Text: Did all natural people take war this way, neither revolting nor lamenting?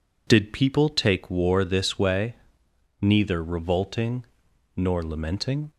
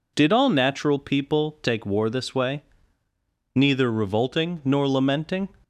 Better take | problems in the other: second | skips "all natural"; at 0.5 s // pauses between "revolting" and "nor"; noticeable; at 4.2 s; 0.50 s long

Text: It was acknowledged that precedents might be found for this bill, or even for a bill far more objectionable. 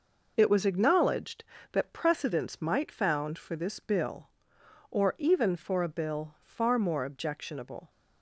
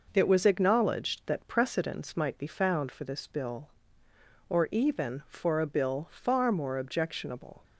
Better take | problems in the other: second | skips "be"; at 2.9 s

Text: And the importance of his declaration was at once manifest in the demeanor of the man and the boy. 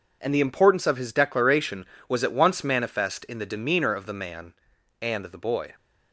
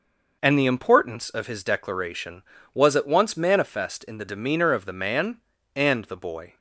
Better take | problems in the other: neither | none

